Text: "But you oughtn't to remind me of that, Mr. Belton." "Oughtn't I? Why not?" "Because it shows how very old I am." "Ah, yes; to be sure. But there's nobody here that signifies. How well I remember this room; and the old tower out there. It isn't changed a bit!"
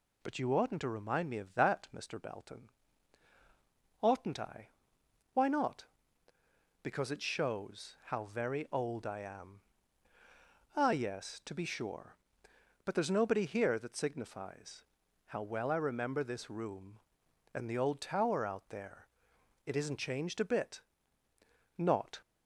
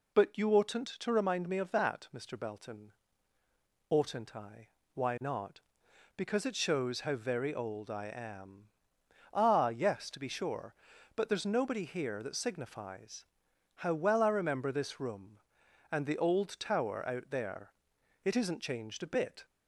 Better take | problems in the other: second | goes on to say "Not"; slight; from 21.7 s on; 0.44 s long

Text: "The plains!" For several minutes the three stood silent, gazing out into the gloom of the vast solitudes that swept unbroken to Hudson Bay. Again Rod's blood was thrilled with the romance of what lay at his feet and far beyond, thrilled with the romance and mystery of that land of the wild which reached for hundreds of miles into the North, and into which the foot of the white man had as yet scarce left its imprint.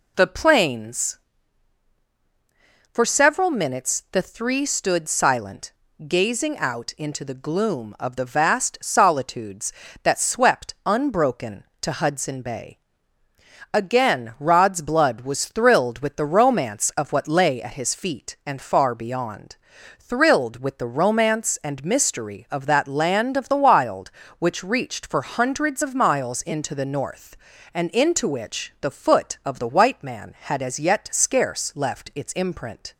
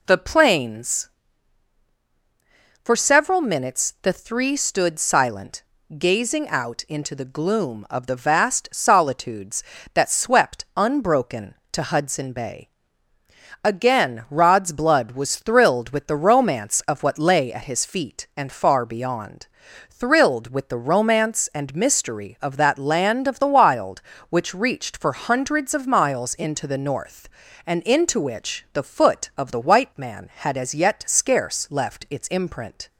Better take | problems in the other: neither | none

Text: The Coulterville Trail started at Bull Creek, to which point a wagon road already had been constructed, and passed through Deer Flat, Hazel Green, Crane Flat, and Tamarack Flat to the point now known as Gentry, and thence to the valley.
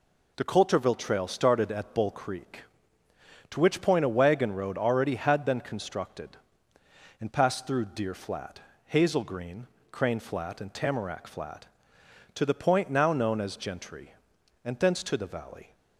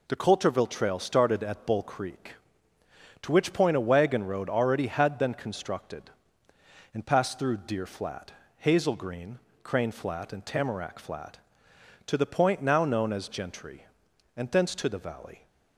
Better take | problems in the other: neither | none

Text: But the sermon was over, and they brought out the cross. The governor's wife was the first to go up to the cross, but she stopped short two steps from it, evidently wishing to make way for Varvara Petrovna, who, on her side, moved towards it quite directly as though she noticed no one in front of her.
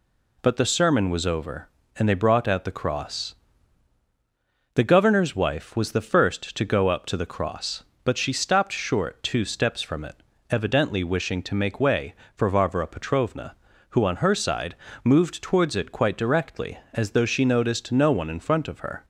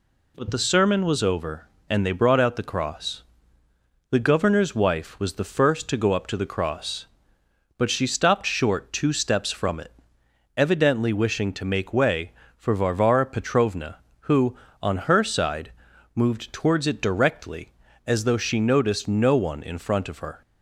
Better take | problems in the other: first | skips "quite"; at 17.0 s

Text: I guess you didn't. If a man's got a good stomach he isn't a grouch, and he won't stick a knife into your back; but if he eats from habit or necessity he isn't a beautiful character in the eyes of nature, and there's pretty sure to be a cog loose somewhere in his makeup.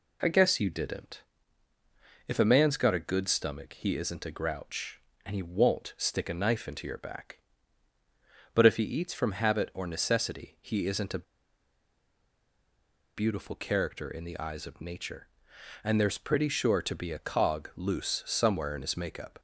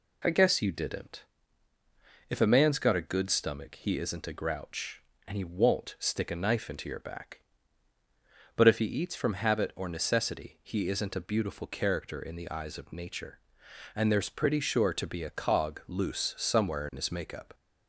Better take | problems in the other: second | pauses between "a" and "beautiful"; strong; at 11.2 s; 1.9 s long

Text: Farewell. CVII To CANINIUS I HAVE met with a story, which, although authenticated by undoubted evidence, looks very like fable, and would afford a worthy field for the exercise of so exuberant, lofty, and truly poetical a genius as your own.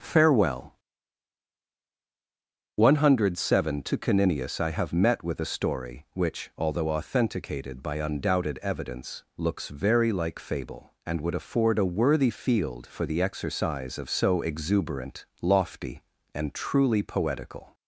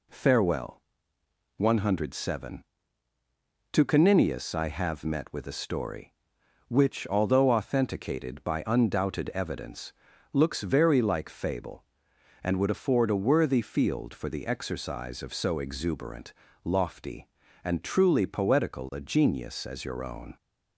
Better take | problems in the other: second | starts louder than the rest; until 3.0 s; 6 dB // stops before "a genius as your own"; at 17.7 s

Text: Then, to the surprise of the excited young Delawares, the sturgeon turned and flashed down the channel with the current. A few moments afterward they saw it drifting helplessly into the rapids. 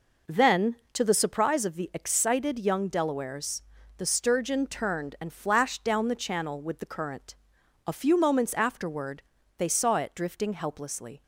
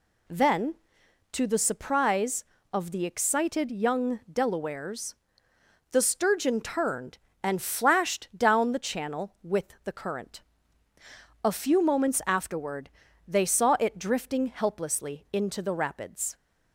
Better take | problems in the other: second | pauses between "afterward" and "they"; slight; at 9.2 s; 0.36 s long; also in the second // stops before "into the rapids"; at 11.2 s

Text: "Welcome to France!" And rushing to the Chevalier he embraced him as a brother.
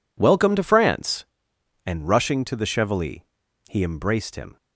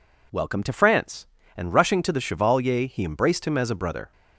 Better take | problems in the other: second | pauses between "Chevalier" and "he"; noticeable; at 3.2 s; 0.48 s long // stops before "as a brother"; at 4.5 s

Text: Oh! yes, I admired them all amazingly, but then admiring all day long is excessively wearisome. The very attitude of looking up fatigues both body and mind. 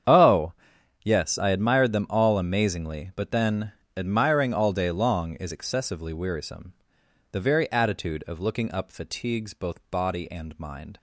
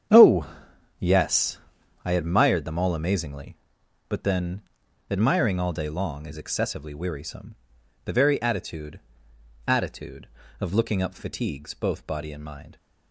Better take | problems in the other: first | starts louder than the rest; strong; until 2.1 s; 8.5 dB; strong in the first // pauses between "then" and "admiring"; noticeable; at 4.6 s; 0.50 s long; slight in the first // says "attitude" twice; at 9.6 s

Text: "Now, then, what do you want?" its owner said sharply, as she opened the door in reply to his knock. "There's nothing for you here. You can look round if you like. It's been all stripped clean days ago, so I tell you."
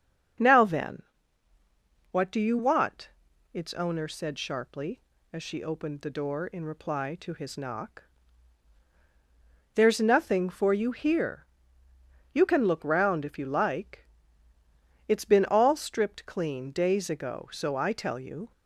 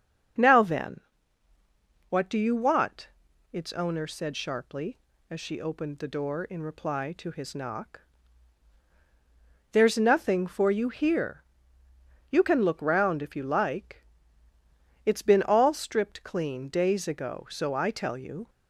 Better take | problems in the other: neither | starts louder than the rest; the same in both

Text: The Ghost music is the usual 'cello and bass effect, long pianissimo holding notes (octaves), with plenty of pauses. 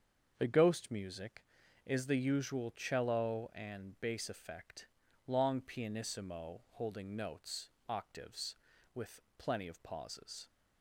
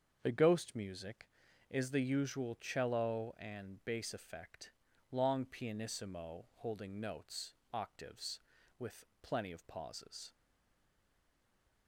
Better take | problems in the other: first | starts louder than the rest; until 1.2 s; 7 dB; also in the first // pauses between "with" and "plenty"; slight; at 9.0 s; 0.16 s long; slight in the first // stays silent after the last word; noticeable; from 10.3 s on; 1.5 s long

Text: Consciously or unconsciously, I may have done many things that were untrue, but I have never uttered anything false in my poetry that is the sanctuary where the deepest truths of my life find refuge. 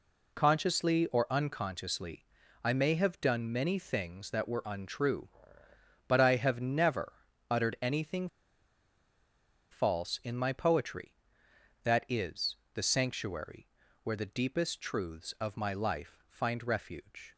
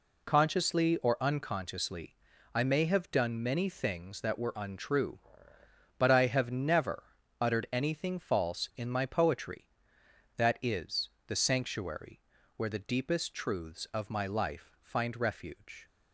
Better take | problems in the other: second | pauses between "never" and "uttered"; at 7.1 s; 0.38 s long; also in the second // pauses between "anything" and "false"; strong; at 8.2 s; 1.4 s long // pauses between "is" and "the"; slight; at 12.5 s; 0.18 s long; slight in the second // pauses between "sanctuary" and "where"; slight; at 13.6 s; 0.36 s long; slight in the second

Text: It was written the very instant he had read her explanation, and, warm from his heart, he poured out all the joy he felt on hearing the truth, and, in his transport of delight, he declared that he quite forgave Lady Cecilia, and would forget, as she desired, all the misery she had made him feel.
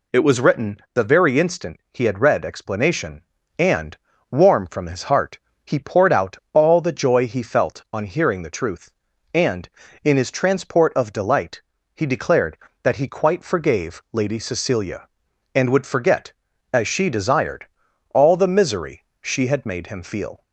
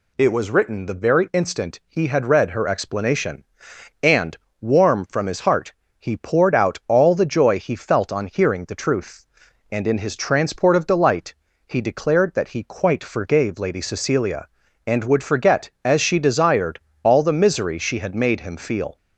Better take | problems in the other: second | skips "her"; at 2.4 s // pauses between "out" and "all"; slight; at 6.3 s; 0.16 s long // pauses between "misery" and "she"; slight; at 19.0 s; 0.18 s long

